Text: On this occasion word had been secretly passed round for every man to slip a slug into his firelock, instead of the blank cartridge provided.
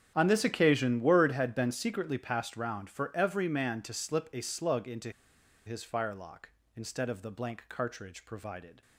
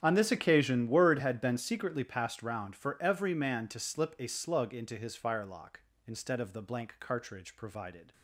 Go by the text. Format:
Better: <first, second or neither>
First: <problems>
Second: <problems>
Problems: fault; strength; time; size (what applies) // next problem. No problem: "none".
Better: second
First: starts louder than the rest; strong; until 1.1 s; 9 dB // pauses between "into" and "his"; noticeable; at 5.0 s; 0.56 s long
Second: starts louder than the rest; strong; until 1.0 s; 9.5 dB